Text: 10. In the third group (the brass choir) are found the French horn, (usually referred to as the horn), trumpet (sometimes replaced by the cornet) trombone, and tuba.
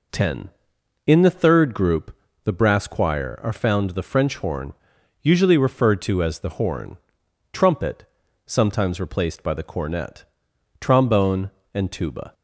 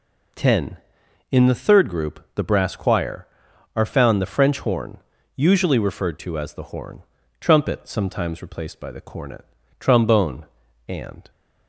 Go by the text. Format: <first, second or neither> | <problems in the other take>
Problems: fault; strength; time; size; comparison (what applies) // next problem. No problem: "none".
first | stops before "tuba"; at 11.3 s